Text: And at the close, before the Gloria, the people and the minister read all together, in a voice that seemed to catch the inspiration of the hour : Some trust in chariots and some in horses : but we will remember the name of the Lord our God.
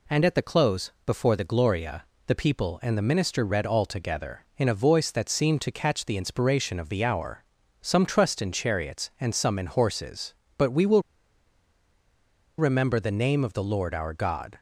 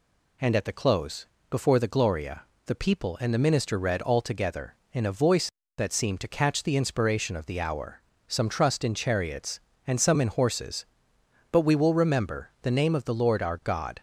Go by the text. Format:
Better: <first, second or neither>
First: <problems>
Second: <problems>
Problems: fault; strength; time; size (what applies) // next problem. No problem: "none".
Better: second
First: pauses between "will" and "remember"; strong; at 11.0 s; 1.5 s long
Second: none